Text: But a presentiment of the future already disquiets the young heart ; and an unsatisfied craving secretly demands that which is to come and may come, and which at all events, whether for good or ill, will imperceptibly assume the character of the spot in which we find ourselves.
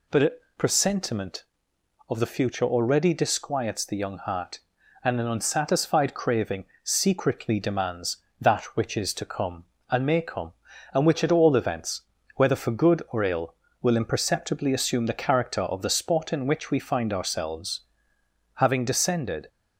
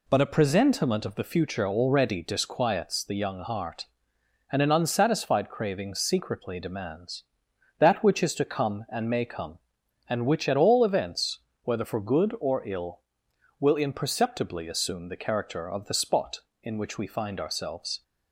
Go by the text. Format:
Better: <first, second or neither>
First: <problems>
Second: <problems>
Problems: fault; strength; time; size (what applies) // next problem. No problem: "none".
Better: second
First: pauses between "a" and "presentiment"; slight; at 0.3 s; 0.24 s long // pauses between "craving" and "secretly"; slight; at 6.6 s; 0.18 s long // goes on to say "Having descended"; noticeable; from 18.5 s on; 0.94 s long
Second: none